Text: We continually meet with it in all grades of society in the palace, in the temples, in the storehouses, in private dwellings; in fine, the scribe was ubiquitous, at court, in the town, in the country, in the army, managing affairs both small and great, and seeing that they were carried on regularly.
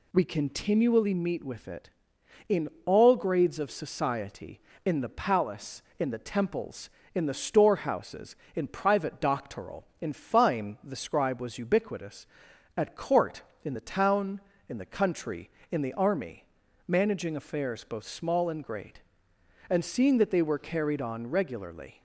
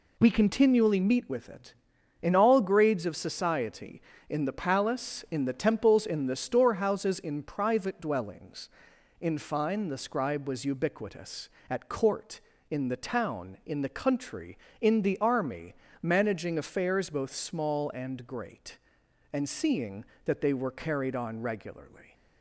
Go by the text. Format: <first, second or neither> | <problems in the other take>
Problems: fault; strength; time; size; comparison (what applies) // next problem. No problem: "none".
second | pauses between "in" and "all"; slight; at 2.6 s; 0.16 s long // says "doctoral" for "dwellings"; at 9.2 s